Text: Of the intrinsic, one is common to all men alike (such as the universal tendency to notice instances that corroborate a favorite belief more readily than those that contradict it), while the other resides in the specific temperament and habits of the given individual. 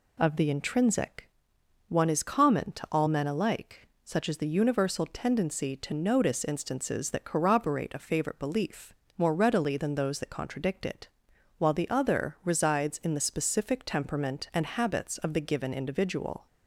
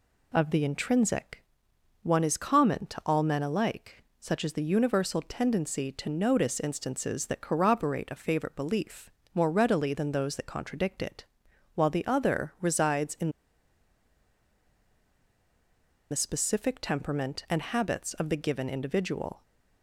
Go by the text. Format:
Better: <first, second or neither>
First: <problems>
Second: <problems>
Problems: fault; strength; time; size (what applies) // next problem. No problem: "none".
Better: first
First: pauses between "belief" and "more"; slight; at 8.9 s; 0.24 s long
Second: pauses between "belief" and "more"; slight; at 9.1 s; 0.24 s long // pauses between "in" and "the"; strong; at 13.2 s; 2.8 s long